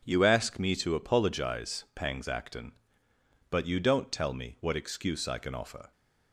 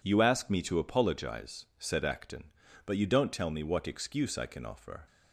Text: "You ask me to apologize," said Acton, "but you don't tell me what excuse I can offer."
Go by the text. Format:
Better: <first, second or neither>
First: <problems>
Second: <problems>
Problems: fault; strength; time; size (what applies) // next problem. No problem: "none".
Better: second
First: says "pangs" for "said"; at 1.9 s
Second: none